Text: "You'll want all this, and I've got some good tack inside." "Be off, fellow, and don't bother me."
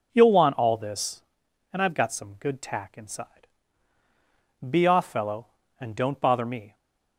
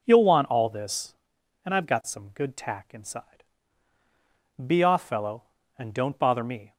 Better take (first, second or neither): neither